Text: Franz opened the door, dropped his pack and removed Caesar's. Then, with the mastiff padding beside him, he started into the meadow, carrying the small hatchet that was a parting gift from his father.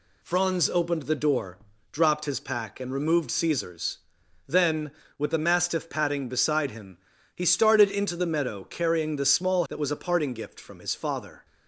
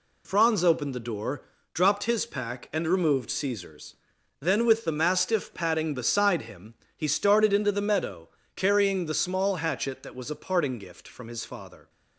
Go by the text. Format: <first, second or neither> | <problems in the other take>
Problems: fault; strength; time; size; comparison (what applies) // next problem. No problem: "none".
second | skips "hatchet"; at 9.6 s